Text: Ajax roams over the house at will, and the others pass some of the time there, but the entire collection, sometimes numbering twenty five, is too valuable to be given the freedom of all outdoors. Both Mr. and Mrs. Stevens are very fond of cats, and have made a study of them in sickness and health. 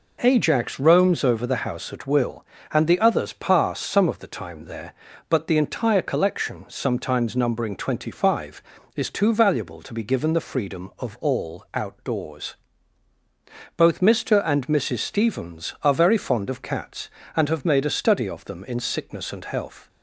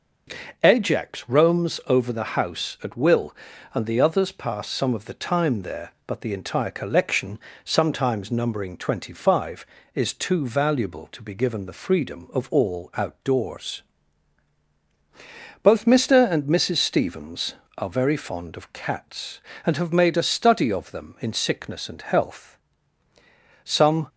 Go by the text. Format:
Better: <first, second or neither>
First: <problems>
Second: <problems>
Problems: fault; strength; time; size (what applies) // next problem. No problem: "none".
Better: first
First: none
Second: goes on to say "Some"; slight; from 23.6 s on; 0.44 s long